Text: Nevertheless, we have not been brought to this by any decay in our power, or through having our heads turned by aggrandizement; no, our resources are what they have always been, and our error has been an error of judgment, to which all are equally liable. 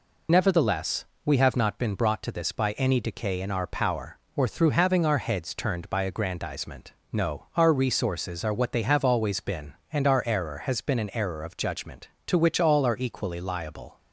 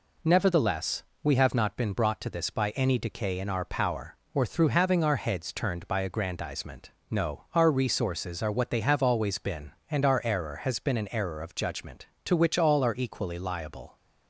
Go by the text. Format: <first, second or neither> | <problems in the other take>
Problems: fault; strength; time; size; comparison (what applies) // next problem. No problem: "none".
second | loses the start of "Nevertheless"; at 0.2 s; 80 ms